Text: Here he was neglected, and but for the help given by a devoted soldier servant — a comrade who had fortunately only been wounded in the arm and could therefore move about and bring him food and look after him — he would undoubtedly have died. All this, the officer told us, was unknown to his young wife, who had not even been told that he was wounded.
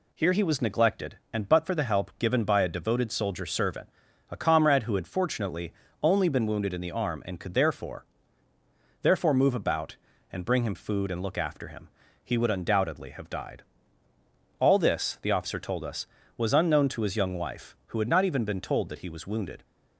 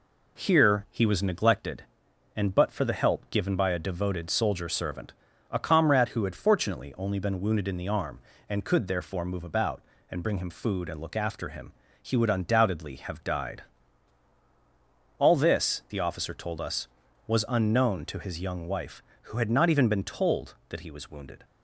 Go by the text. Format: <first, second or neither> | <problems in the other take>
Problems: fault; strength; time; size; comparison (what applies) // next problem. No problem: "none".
second | pauses between "fortunately" and "only"; slight; at 5.7 s; 0.30 s long // says "therefore" twice; at 9.0 s